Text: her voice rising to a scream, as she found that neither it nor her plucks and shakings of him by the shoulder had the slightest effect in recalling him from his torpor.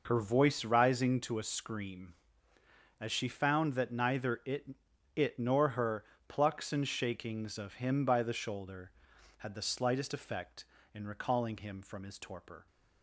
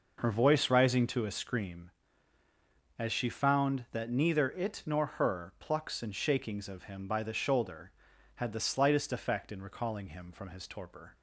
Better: second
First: says "it" twice; at 5.1 s // pauses between "her" and "plucks"; slight; at 6.0 s; 0.24 s long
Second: none

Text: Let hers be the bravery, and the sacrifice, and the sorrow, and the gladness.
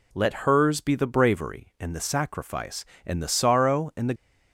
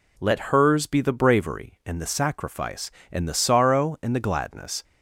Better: second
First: stops before "gladness"; at 4.1 s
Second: none

